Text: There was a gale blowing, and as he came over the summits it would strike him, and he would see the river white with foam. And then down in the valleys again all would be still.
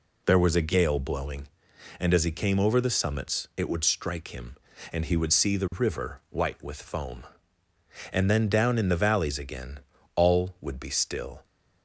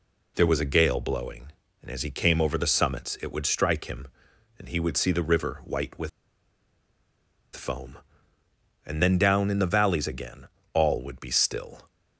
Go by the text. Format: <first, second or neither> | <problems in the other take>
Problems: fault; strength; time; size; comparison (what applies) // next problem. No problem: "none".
first | pauses between "with" and "foam"; strong; at 6.0 s; 1.4 s long // pauses between "again" and "all"; slight; at 10.4 s; 0.28 s long; slight in the first